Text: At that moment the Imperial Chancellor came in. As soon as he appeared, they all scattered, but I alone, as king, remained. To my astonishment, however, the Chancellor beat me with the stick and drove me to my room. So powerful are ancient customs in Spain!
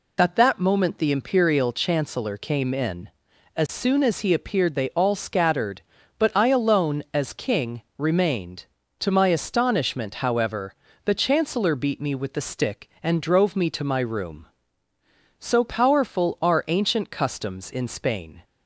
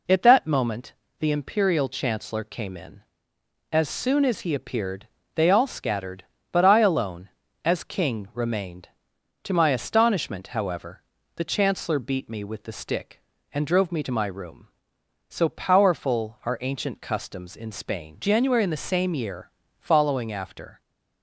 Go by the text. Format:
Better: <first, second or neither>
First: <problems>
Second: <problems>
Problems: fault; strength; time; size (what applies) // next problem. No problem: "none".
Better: first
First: none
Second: pauses between "moment" and "the"; slight; at 0.9 s; 0.24 s long // goes on to say "January in the same year following after"; strong; from 18.1 s on; 2.6 s long